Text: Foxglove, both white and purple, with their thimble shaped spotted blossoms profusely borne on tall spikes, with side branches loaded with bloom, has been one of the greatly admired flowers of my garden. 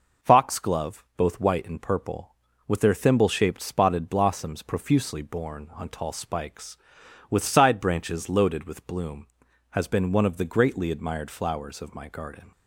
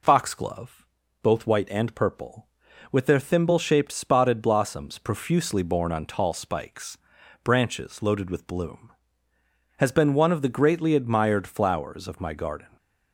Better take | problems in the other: first | skips "with side"; at 7.2 s

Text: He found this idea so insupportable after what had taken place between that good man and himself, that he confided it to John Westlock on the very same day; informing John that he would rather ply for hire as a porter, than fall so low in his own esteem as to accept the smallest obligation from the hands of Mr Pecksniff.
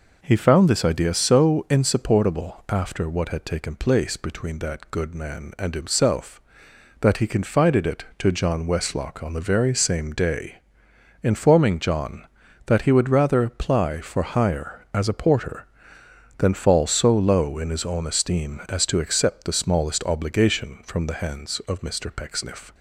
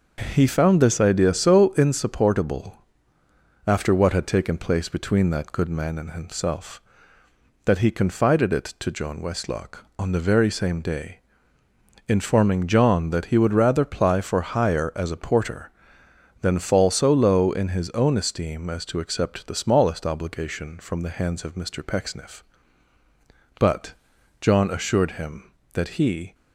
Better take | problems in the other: first | starts louder than the rest; noticeable; until 1.3 s; 6 dB // pauses between "insupportable" and "after"; noticeable; at 2.7 s; 0.92 s long // goes on to say "But John assured him that he"; strong; from 23.6 s on; 2.7 s long

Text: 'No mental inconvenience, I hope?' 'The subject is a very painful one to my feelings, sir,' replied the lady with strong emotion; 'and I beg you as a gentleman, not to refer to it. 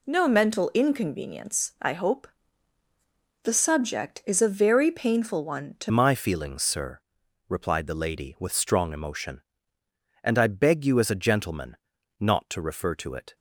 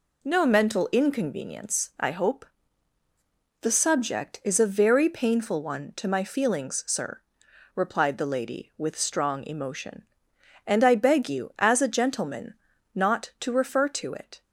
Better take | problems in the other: second | changes voice at "my"; from 5.9 s on; 7.4 s long

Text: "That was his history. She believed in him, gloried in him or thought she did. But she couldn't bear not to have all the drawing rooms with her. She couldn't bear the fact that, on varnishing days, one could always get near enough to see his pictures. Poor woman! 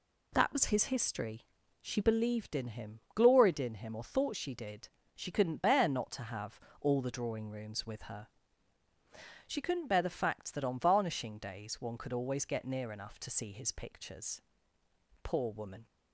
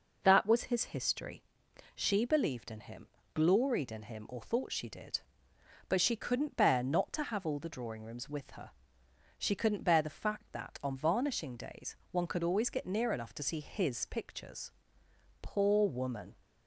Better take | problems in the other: second | skips "But"; at 5.0 s // pauses between "have" and "all"; slight; at 6.5 s; 0.22 s long

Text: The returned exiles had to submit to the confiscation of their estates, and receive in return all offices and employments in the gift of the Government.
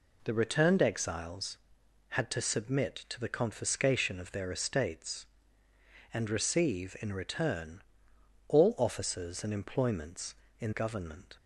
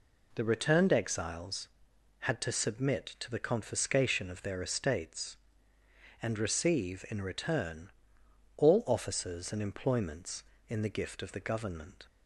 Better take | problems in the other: second | pauses between "return" and "all"; noticeable; at 7.8 s; 0.66 s long; noticeable in the second // skips "the gift of the"; at 10.7 s

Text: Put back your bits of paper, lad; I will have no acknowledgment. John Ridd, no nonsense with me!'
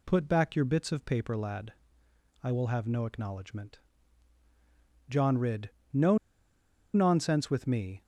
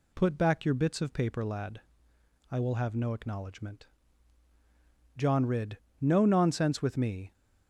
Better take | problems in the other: second | pauses between "no" and "nonsense"; noticeable; at 6.1 s; 0.76 s long

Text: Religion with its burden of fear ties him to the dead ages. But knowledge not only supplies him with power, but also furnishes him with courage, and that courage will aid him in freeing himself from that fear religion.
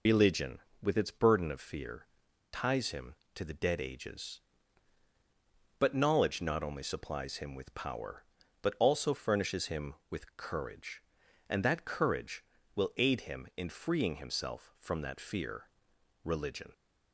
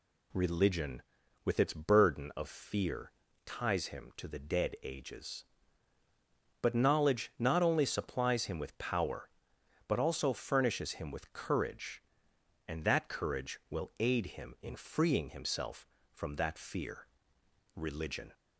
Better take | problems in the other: second | loses the start of "Religion"; at 0.0 s; 125 ms // pauses between "fear" and "ties"; noticeable; at 2.0 s; 0.46 s long; slight in the second // pauses between "fear" and "religion"; noticeable; at 15.6 s; 0.58 s long; noticeable in the second

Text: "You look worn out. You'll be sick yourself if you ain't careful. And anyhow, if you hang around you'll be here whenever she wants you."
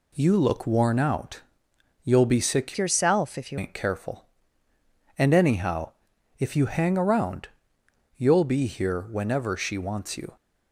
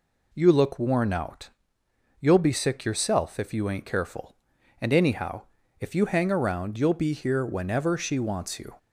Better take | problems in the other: second | changes voice from "yourself" to "you"; from 2.7 to 3.5 s; 0.8 s long // pauses between "around" and "you'll"; noticeable; at 7.4 s; 0.70 s long

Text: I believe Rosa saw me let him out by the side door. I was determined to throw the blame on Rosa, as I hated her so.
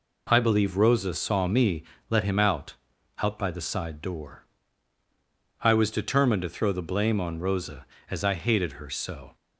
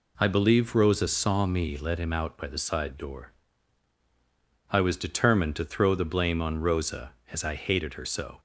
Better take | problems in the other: second | pauses between "me" and "let"; slight; at 1.8 s; 0.26 s long // says "out" twice; at 3.1 s

